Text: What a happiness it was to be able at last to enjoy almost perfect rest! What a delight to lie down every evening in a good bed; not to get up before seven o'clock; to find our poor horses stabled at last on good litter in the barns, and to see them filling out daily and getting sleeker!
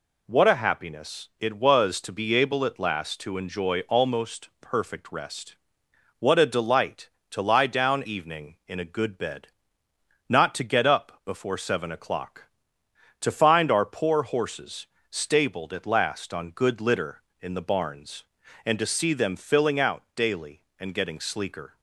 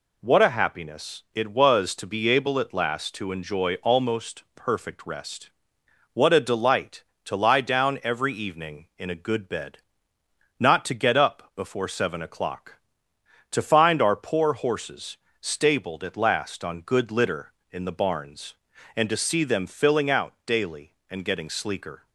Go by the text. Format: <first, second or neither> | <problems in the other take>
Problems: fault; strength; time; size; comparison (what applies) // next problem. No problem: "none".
second | skips "every"; at 8.0 s // pauses between "horses" and "stabled"; slight; at 14.8 s; 0.24 s long; slight in the second